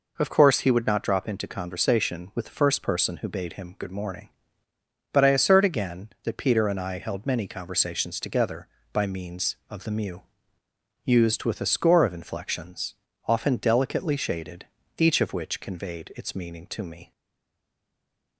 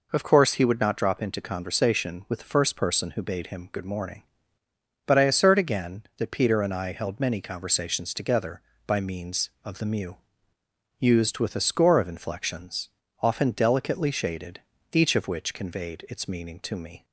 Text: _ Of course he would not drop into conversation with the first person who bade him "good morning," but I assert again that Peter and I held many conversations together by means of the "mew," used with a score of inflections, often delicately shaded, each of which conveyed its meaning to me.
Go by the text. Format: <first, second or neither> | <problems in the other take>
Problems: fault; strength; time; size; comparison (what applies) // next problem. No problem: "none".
second | stays silent after the last word; noticeable; from 17.1 s on; 1.2 s long